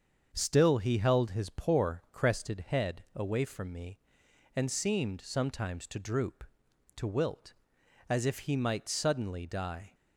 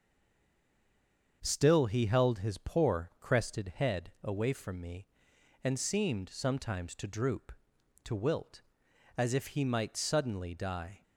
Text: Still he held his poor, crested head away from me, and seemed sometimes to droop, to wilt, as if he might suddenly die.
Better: first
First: starts louder than the rest; until 1.3 s; 6.5 dB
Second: stays silent before the first word; noticeable; until 1.4 s; 1.4 s long // starts louder than the rest; until 2.4 s; 7 dB

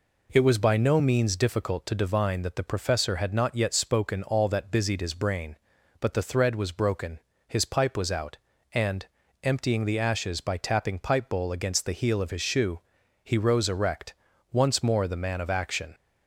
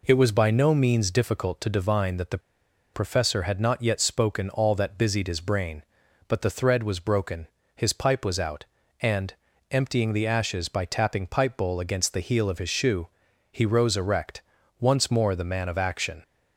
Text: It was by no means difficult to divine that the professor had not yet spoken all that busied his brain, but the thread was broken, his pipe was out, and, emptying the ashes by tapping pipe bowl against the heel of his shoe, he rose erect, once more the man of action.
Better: first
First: none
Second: pauses between "the" and "professor"; noticeable; at 2.3 s; 0.55 s long

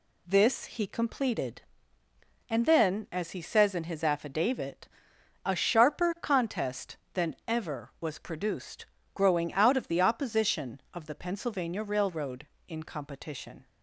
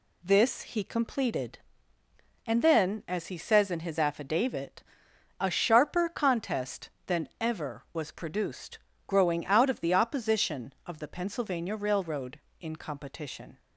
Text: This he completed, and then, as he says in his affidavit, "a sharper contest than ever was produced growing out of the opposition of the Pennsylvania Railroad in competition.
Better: neither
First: pauses between "produced" and "growing"; slight; at 8.8 s; 0.26 s long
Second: pauses between "produced" and "growing"; slight; at 8.7 s; 0.26 s long

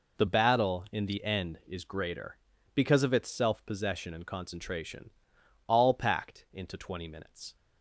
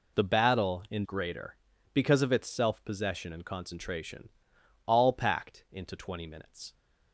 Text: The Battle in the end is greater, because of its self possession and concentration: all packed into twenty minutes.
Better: first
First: none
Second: skips "the end is"; at 1.0 s

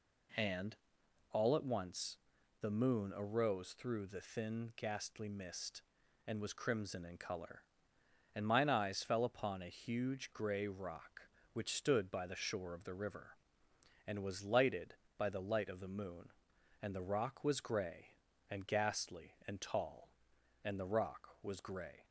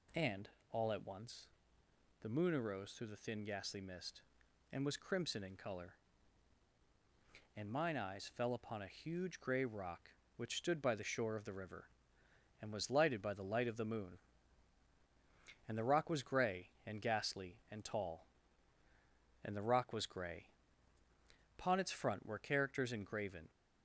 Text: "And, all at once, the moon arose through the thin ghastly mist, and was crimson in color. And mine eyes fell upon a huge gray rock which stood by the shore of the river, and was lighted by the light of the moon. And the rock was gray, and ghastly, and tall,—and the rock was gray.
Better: first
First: none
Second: goes on to say "Upon its front were characters engraven"; strong; from 21.5 s on; 1.9 s long

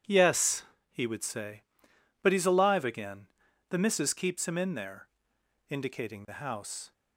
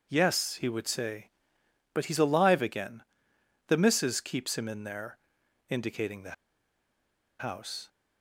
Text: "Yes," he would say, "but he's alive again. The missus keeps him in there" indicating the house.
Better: first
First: pauses between "there" and "indicating"; noticeable; at 5.0 s; 0.62 s long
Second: pauses between "there" and "indicating"; noticeable; at 5.1 s; 0.52 s long // pauses between "the" and "house"; at 6.3 s; 1.0 s long

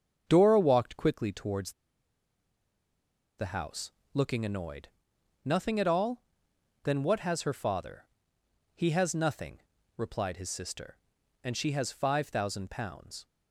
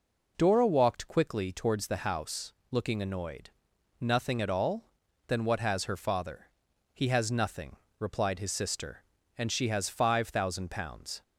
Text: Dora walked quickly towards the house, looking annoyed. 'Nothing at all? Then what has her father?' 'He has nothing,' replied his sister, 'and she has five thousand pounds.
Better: second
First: starts louder than the rest; until 1.2 s; 7 dB // pauses between "towards" and "the"; strong; at 1.7 s; 1.6 s long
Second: none

